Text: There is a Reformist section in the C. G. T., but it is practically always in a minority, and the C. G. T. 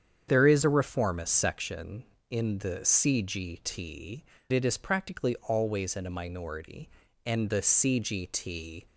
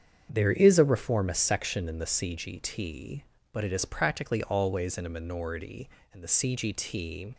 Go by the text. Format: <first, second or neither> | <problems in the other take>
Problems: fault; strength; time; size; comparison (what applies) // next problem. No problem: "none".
second | starts louder than the rest; strong; until 1.3 s; 8 dB; strong in the second // skips "but"; at 4.3 s